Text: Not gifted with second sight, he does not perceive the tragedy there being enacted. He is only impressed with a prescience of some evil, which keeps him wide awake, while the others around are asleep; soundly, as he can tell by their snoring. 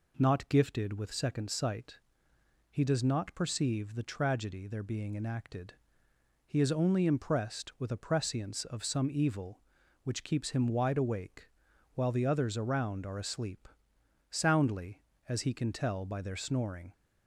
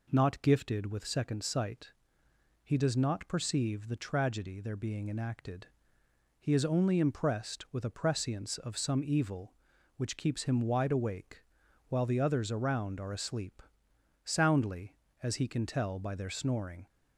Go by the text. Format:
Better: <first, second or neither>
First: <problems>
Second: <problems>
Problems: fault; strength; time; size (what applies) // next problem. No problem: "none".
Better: neither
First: none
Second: none